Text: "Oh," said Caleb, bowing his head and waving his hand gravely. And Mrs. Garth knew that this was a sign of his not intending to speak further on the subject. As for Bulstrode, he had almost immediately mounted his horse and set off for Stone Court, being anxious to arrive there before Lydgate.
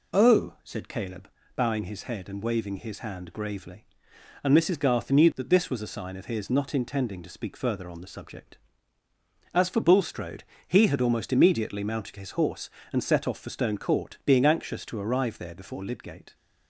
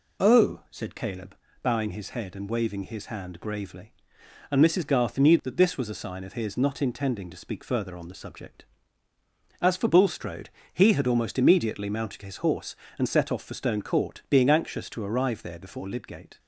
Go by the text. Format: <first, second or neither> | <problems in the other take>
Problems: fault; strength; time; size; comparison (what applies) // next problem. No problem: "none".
neither | none